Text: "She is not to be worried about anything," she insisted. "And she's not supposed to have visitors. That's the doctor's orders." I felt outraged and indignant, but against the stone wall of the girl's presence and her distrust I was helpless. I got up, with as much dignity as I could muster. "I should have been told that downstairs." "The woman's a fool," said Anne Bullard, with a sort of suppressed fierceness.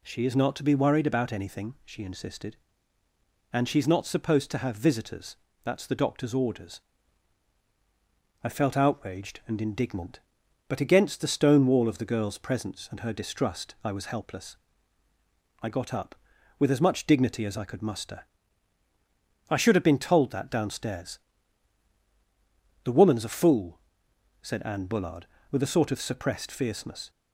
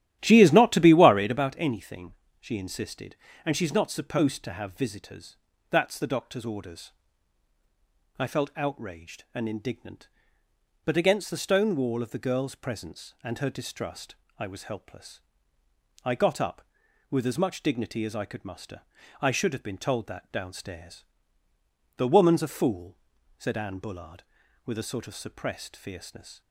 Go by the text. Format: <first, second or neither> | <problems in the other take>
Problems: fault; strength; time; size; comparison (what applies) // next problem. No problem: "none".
first | starts louder than the rest; strong; until 1.5 s; 12.5 dB // pauses between "distrust" and "I"; slight; at 14.1 s; 0.20 s long